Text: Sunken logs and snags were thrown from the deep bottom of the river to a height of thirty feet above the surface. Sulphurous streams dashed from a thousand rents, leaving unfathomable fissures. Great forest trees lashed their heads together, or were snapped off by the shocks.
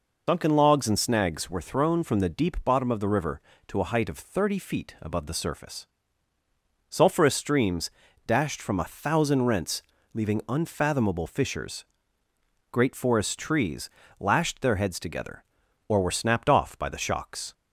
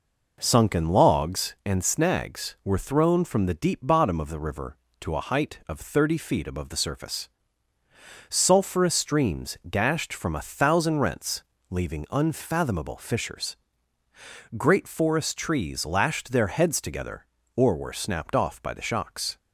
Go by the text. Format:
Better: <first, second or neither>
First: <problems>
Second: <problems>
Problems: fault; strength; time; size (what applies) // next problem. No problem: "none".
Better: second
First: loses the start of "Sunken"; at 0.2 s; 100 ms // pauses between "streams" and "dashed"; slight; at 7.9 s; 0.34 s long // pauses between "trees" and "lashed"; slight; at 13.8 s; 0.30 s long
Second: none